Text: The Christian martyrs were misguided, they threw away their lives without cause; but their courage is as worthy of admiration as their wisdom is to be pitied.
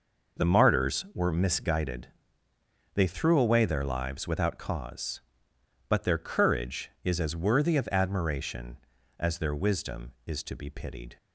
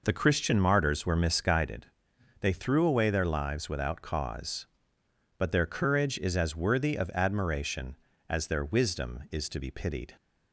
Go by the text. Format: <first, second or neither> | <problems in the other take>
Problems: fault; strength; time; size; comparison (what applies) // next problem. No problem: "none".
second | skips "Christian"; at 0.4 s